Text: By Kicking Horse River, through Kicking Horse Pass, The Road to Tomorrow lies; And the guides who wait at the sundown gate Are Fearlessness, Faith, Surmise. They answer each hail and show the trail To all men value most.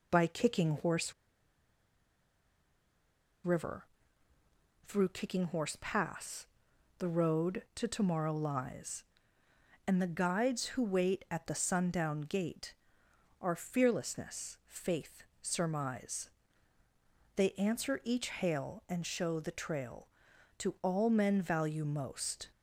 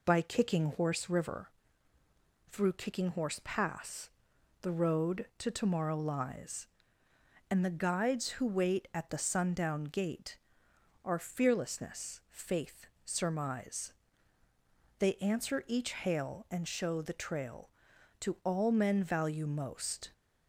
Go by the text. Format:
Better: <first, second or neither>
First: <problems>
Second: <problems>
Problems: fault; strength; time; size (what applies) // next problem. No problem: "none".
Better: second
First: pauses between "Horse" and "River"; strong; at 1.1 s; 2.3 s long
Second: none